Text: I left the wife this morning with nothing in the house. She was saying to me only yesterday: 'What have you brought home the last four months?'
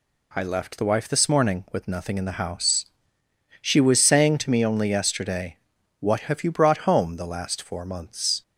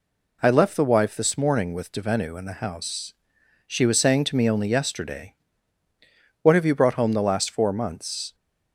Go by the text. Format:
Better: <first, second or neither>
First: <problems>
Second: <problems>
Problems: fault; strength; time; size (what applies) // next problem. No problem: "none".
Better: first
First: none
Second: says "devenu" for "nothing"; at 1.9 s